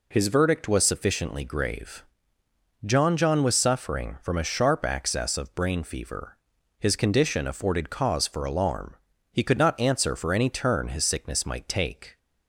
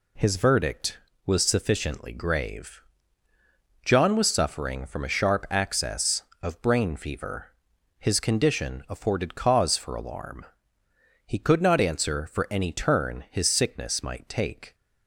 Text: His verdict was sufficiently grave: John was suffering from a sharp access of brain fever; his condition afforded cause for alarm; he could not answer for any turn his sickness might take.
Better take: second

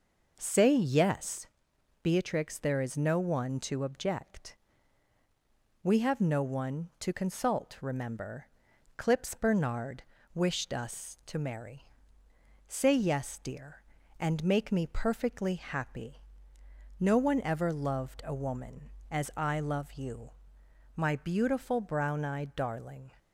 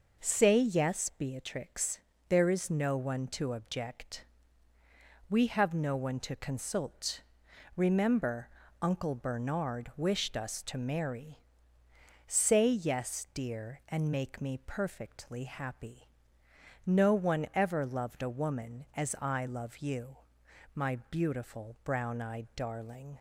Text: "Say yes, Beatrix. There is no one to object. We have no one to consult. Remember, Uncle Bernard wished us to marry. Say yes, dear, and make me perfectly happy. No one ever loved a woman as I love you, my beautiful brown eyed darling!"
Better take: second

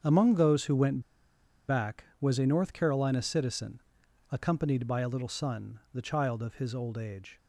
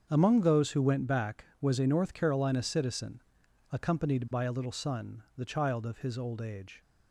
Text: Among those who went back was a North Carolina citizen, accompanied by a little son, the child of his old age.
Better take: second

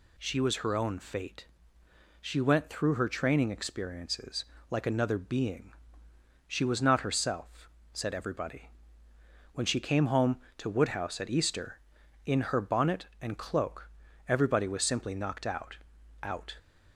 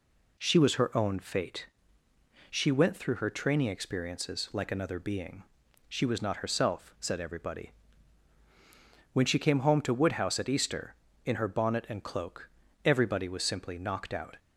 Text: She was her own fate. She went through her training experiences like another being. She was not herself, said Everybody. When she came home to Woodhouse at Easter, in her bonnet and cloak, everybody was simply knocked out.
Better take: second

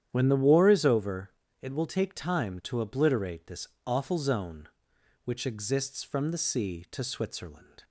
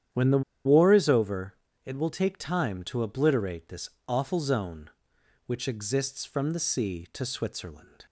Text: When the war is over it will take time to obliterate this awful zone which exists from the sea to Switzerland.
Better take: first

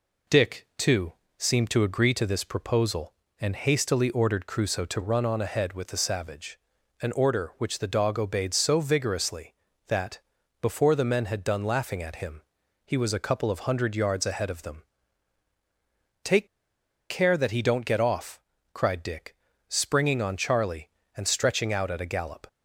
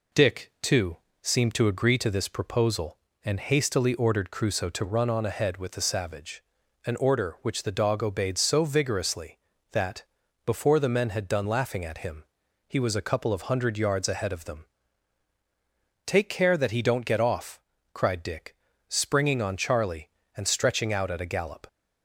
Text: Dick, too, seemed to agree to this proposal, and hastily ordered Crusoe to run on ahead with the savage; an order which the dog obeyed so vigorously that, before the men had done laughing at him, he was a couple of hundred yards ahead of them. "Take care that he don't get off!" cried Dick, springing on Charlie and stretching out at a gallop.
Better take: second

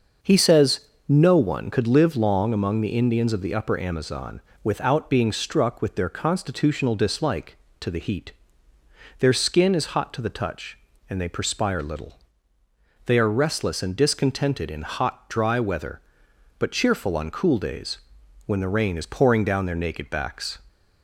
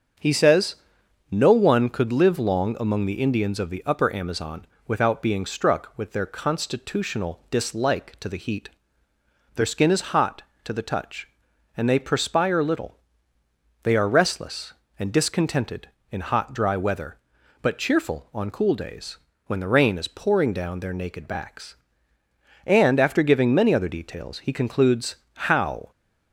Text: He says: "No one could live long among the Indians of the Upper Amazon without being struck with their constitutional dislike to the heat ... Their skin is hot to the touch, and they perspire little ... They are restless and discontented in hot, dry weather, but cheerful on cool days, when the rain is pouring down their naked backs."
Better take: first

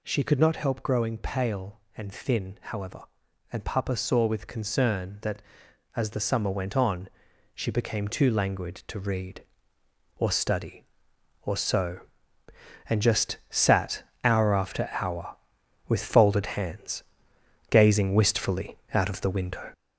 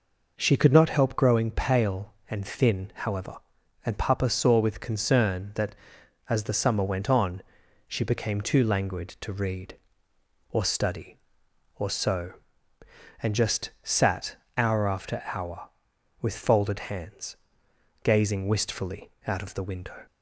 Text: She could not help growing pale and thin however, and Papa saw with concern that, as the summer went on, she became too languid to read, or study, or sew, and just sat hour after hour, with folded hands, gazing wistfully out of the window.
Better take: second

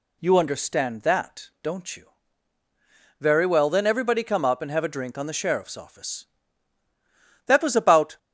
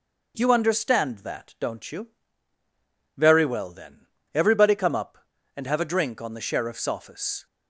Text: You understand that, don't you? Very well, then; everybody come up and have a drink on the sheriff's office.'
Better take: second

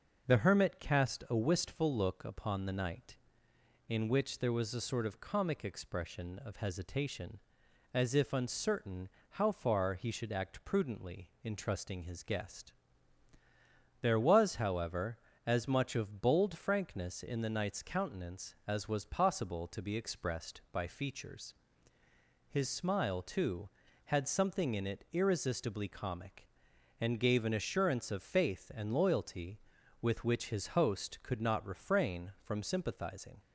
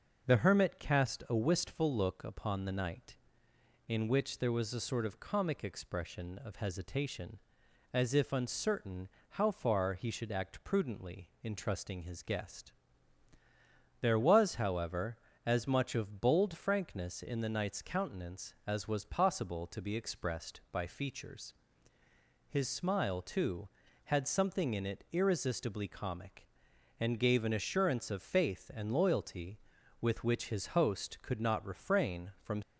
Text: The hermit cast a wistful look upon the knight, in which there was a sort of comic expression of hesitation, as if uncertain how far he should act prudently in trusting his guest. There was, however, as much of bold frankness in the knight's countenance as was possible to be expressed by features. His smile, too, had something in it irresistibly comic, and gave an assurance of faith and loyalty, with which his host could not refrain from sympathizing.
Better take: first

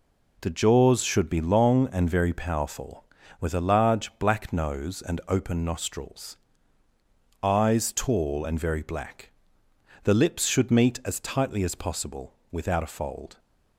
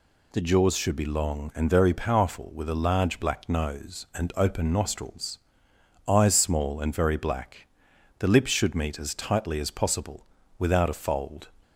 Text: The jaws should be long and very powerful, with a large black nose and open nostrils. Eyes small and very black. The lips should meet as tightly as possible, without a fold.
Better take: second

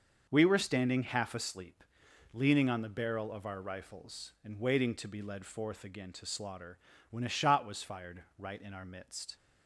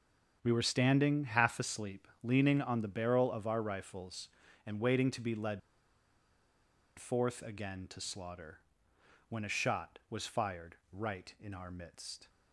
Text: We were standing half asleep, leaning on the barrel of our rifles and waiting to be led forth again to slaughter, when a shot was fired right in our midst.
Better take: first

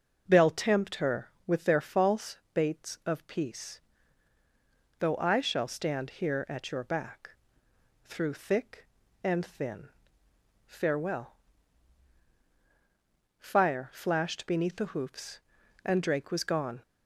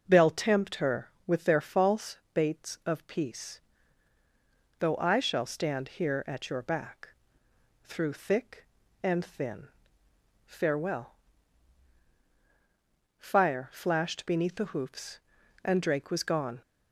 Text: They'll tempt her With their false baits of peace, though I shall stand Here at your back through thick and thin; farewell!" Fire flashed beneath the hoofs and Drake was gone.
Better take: neither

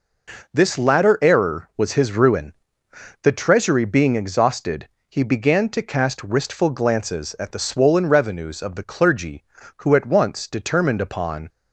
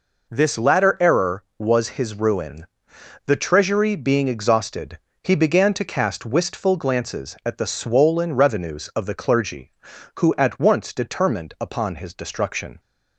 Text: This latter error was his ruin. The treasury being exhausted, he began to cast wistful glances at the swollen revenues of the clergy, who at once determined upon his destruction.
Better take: second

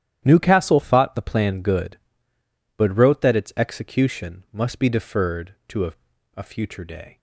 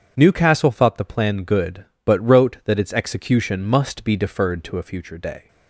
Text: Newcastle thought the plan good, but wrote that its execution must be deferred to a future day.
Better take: second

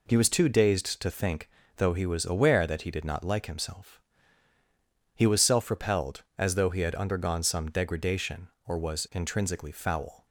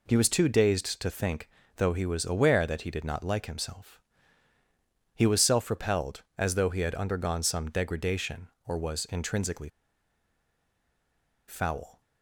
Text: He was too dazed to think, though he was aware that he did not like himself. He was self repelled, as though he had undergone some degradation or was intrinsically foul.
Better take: first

